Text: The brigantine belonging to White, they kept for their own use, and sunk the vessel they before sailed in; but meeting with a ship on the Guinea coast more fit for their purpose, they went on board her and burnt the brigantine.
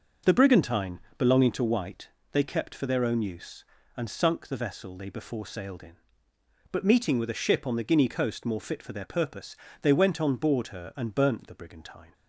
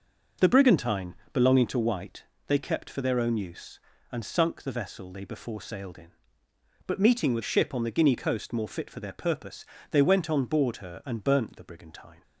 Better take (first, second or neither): first